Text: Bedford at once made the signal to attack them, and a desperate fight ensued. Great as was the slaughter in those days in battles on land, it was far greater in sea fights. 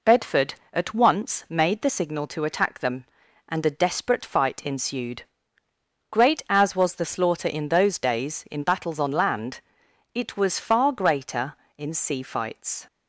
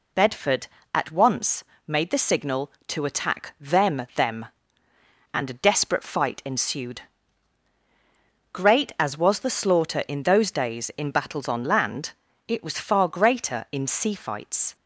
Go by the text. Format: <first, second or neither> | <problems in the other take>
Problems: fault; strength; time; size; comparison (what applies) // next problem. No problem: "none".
first | pauses between "once" and "made"; slight; at 1.6 s; 0.24 s long // says "them" twice; at 4.1 s